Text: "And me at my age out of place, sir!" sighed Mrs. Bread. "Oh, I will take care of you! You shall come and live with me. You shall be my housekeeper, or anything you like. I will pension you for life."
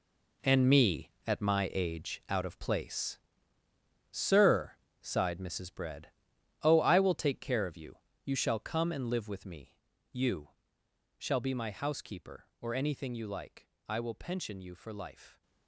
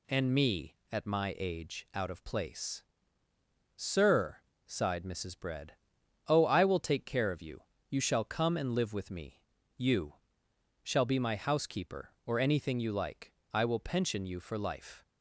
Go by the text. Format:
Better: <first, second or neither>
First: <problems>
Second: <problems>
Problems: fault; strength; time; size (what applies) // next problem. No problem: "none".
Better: second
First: gets quieter; strong; throughout; 11.5 dB // pauses between "You" and "shall"; noticeable; at 10.4 s; 0.70 s long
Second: pauses between "You" and "shall"; noticeable; at 10.1 s; 0.70 s long